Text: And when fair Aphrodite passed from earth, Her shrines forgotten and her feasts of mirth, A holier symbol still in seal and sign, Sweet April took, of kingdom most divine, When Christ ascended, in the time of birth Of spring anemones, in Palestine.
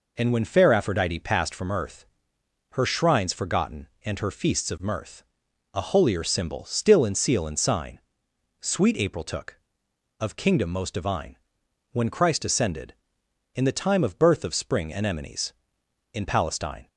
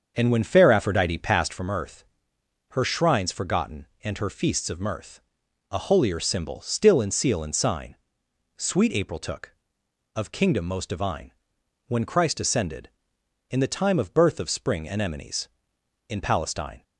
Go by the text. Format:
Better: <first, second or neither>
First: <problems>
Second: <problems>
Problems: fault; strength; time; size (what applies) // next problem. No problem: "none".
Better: first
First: none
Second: starts louder than the rest; until 1.6 s; 7 dB